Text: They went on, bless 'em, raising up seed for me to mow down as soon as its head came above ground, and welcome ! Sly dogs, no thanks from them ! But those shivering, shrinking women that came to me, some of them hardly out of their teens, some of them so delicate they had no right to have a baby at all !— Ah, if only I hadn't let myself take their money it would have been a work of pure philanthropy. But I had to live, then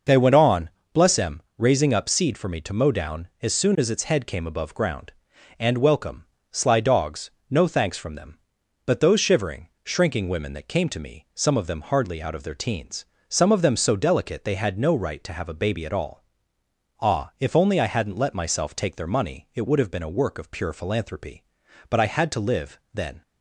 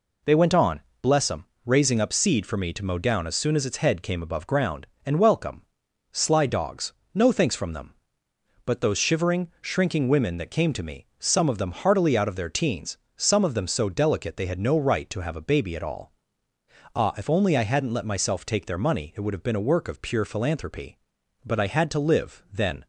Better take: first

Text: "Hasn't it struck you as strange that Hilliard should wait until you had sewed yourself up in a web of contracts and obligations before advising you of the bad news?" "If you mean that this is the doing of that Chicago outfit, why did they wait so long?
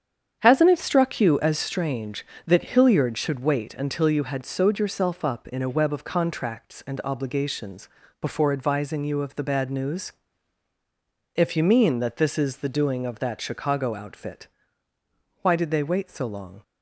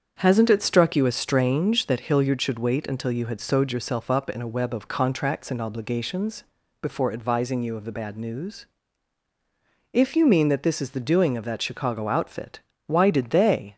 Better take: first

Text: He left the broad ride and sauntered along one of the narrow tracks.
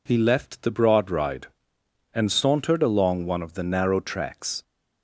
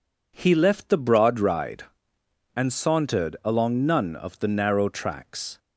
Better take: first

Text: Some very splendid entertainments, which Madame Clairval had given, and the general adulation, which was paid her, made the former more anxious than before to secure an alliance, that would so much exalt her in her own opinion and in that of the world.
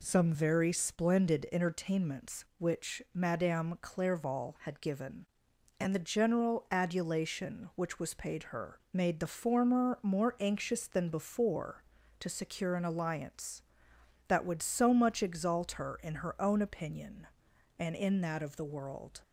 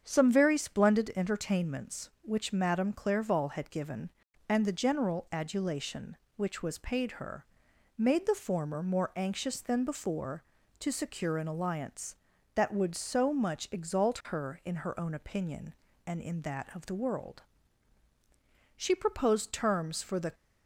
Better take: first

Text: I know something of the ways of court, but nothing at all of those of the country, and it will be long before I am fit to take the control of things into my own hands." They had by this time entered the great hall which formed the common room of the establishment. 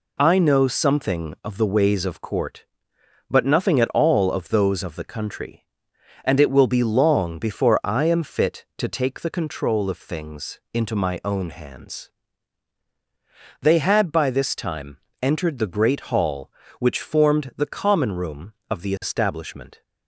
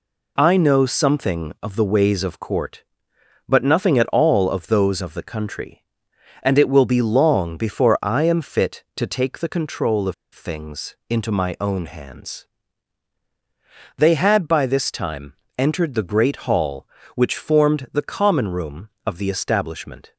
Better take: first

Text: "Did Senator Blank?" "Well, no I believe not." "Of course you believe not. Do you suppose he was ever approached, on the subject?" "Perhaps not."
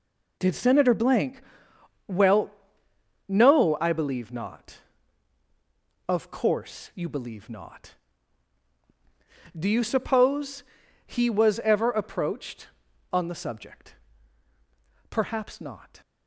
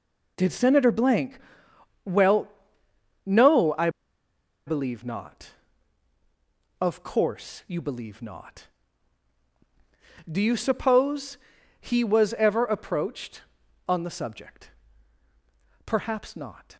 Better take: first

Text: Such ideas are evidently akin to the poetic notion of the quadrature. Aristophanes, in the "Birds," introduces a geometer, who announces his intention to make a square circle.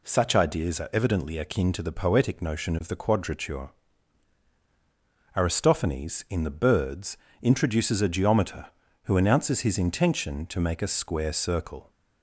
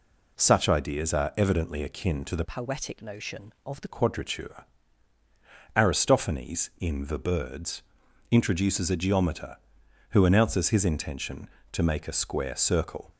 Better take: first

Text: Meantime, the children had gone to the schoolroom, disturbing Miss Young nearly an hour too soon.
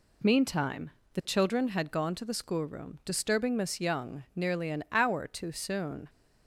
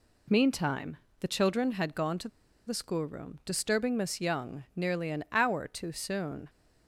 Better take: first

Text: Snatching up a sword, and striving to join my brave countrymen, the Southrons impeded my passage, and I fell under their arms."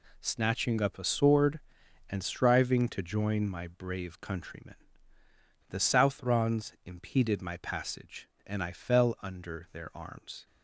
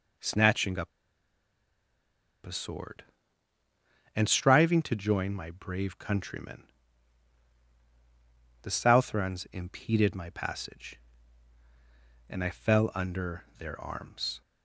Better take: first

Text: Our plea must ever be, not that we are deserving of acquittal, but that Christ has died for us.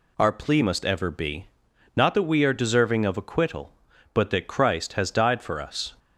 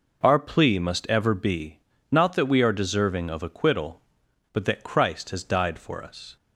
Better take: neither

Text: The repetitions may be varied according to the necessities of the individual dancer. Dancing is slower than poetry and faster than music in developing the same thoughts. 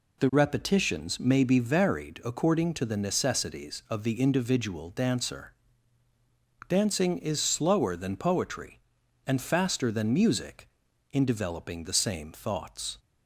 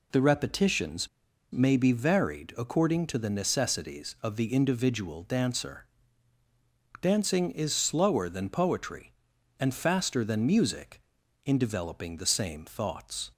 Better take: first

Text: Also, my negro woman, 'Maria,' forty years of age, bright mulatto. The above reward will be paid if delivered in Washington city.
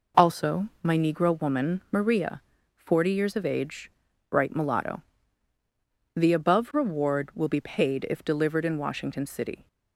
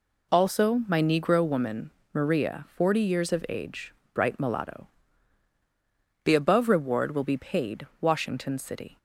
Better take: first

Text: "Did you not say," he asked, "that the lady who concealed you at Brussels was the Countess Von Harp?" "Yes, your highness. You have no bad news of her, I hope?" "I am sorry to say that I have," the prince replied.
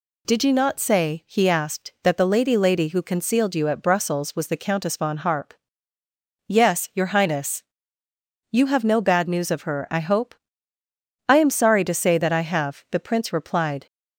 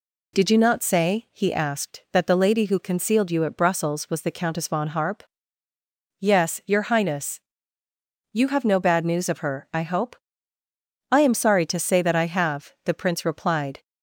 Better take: second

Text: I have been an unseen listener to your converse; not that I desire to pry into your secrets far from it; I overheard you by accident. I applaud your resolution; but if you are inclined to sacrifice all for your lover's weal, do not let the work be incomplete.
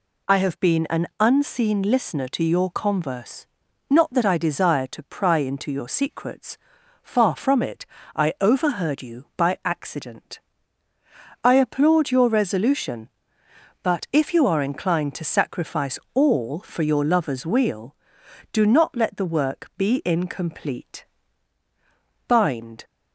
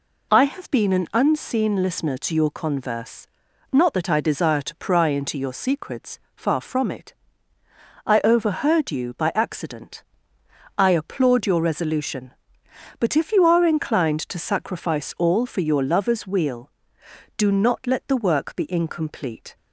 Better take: second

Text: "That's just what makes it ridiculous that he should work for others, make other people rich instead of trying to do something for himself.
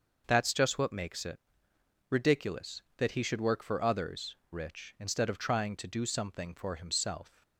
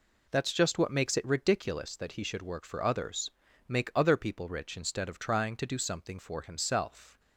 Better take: second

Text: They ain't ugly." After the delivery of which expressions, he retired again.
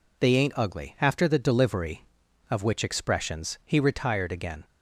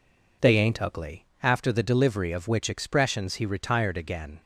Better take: neither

